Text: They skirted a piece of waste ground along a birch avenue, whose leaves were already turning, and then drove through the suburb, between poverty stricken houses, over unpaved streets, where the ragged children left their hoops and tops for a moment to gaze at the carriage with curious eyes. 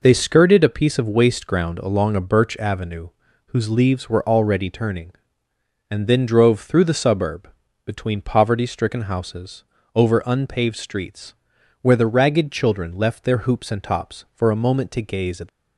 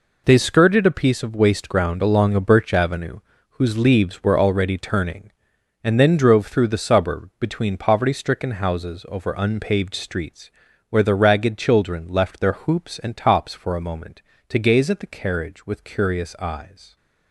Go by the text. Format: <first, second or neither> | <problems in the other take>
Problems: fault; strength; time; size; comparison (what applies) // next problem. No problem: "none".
second | stops before "the carriage with curious eyes"; at 15.4 s